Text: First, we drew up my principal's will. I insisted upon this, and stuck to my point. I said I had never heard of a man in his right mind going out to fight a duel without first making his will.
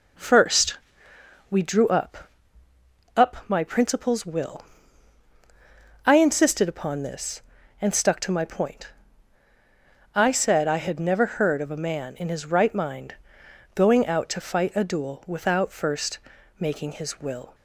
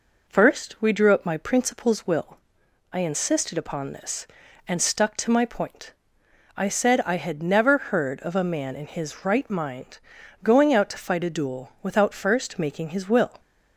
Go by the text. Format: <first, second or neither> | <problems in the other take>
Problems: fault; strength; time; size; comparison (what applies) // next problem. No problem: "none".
second | says "up" twice; at 3.1 s // pauses between "mind" and "going"; noticeable; at 13.1 s; 0.60 s long; also in the second // pauses between "first" and "making"; at 16.1 s; 0.40 s long